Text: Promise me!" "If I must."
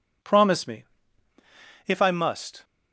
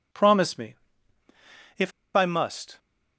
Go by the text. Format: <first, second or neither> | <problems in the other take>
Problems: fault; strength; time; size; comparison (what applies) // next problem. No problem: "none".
first | pauses between "If" and "I"; slight; at 1.9 s; 0.24 s long